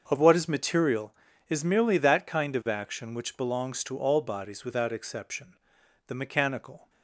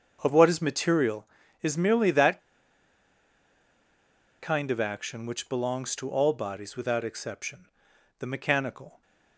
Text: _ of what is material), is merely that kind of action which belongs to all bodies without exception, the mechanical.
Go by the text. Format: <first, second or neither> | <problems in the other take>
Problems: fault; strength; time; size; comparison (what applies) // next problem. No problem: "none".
first | starts louder than the rest; until 1.2 s; 6.5 dB; also in the first // pauses between "that" and "kind"; strong; at 2.3 s; 2.0 s long